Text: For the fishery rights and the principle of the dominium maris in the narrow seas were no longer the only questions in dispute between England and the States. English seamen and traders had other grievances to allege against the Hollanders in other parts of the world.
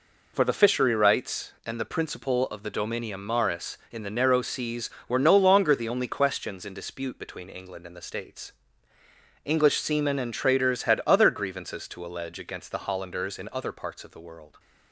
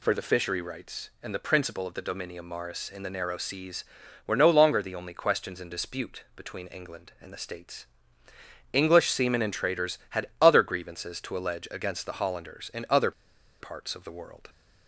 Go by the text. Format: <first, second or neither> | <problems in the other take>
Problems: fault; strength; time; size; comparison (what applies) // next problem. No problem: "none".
first | pauses between "other" and "parts"; noticeable; at 13.1 s; 0.49 s long